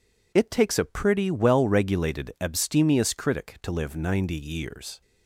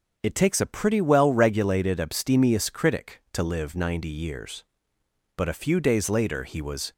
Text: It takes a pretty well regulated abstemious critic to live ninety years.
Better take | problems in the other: first | starts louder than the rest; until 1.2 s; 6.5 dB // goes on to say "But a few days later he was"; from 5.3 s on; 1.5 s long

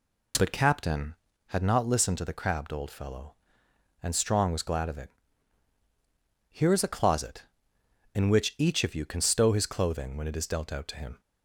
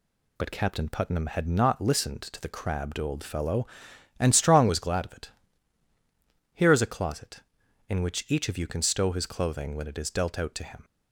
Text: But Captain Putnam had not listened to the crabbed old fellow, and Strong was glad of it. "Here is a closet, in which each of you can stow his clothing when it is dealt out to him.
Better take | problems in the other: second | skips "Putnam"; at 1.3 s

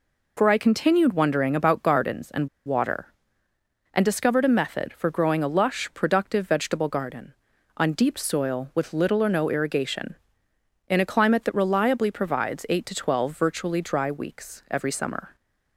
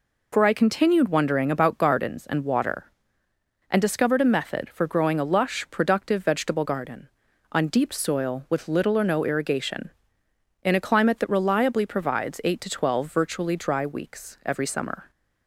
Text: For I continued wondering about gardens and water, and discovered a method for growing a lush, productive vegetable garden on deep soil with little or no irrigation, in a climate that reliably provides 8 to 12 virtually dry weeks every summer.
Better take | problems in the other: second | pauses between "and" and "water"; slight; at 2.4 s; 0.17 s long

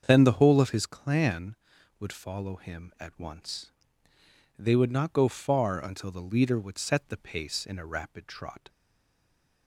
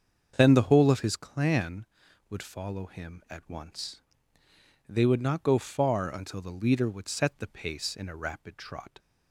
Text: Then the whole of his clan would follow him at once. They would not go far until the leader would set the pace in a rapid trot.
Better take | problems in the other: second | starts louder than the rest; until 1.0 s; 7 dB; also in the second // stays silent after the last word; from 8.6 s on; 1.0 s long

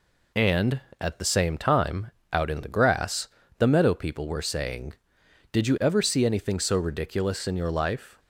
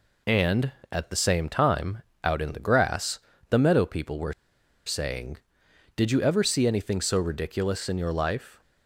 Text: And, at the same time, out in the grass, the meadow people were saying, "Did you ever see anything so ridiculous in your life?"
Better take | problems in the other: first | pauses between "were" and "saying"; noticeable; at 4.3 s; 0.52 s long

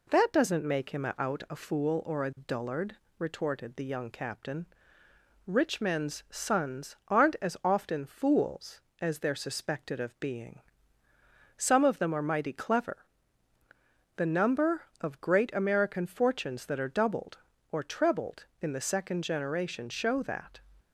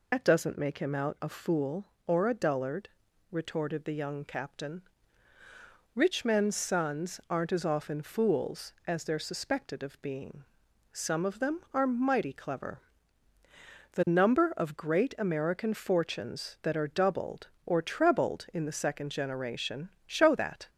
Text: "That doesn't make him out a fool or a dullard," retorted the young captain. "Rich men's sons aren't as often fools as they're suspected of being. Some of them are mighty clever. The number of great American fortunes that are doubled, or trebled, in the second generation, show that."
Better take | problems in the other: first | loses the start of "That"; at 0.1 s; 90 ms

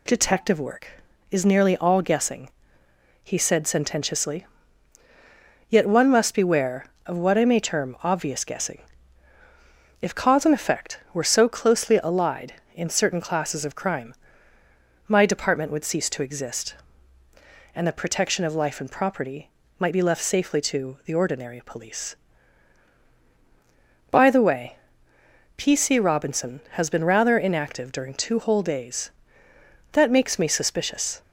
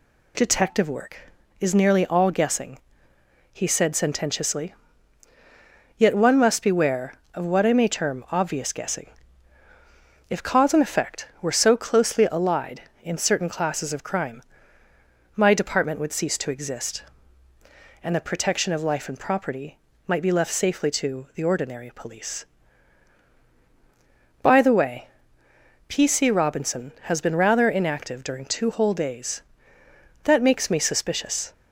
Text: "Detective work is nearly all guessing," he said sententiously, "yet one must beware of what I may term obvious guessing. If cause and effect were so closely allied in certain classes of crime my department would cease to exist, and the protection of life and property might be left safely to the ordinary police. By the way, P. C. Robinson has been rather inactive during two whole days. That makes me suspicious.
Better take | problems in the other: neither | pauses between "crime" and "my"; noticeable; the same in both // pauses between "property" and "might"; slight; the same in both

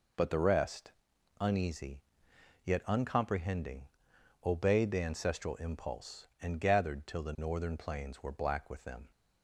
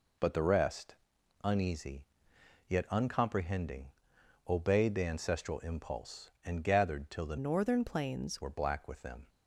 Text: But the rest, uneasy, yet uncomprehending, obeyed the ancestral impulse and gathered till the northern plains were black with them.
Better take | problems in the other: first | changes voice from "northern" to "plains"; from 7.3 to 8.4 s; 1.1 s long

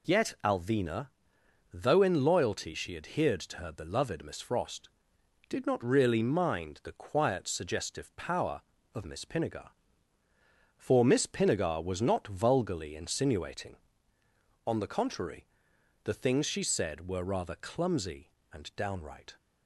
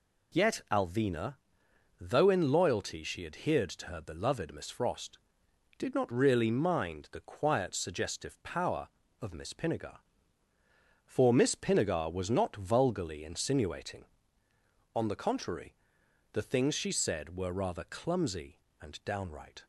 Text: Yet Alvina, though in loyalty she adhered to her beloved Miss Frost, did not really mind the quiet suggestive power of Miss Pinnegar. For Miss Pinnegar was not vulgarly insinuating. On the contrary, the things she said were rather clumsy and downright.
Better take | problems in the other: neither | none

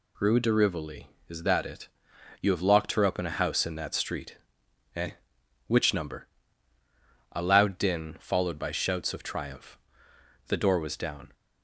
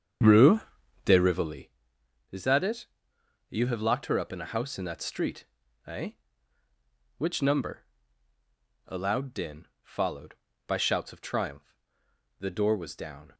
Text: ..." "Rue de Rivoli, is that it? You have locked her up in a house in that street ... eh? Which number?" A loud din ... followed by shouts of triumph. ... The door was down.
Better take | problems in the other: first | starts louder than the rest; strong; until 1.6 s; 7.5 dB // pauses between "Rue" and "de"; at 0.5 s; 0.44 s long

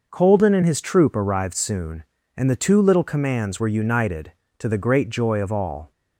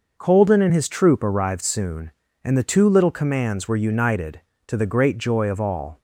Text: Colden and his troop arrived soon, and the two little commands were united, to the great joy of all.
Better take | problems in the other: neither | none

